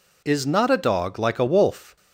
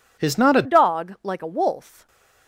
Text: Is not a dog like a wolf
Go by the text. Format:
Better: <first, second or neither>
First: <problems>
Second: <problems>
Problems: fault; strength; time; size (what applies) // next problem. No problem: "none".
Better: first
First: none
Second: changes voice at "dog"; from 0.6 s on; 1.4 s long // stays silent after the last word; slight; from 1.8 s on; 0.6 s long